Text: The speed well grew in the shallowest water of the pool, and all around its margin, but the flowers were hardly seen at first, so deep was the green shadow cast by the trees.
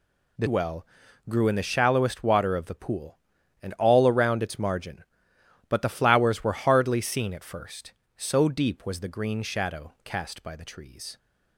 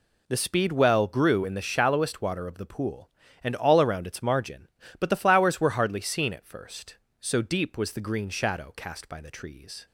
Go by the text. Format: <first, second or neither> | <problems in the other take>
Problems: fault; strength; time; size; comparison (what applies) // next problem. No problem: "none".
second | skips "speed"; at 0.4 s // pauses between "well" and "grew"; at 0.8 s; 0.44 s long